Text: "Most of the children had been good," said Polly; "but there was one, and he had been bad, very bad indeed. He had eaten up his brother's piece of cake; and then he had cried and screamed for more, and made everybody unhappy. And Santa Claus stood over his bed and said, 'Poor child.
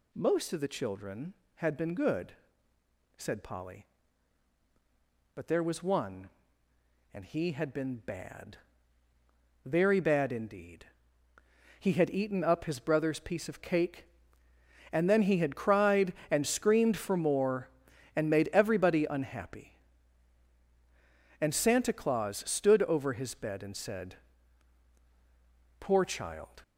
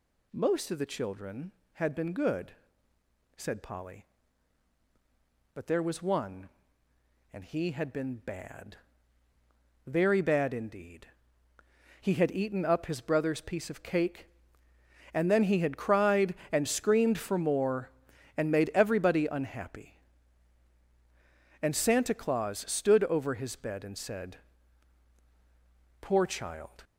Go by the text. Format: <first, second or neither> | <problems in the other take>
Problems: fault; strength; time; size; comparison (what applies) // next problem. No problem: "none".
neither | none